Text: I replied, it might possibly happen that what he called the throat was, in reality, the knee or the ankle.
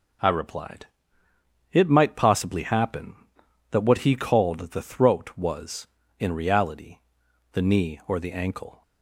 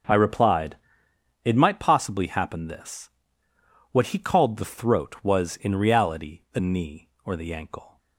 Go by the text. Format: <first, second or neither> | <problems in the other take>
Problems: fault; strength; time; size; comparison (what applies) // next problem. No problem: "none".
first | starts louder than the rest; until 1.7 s; 6.5 dB // says "this" for "that"; at 2.6 s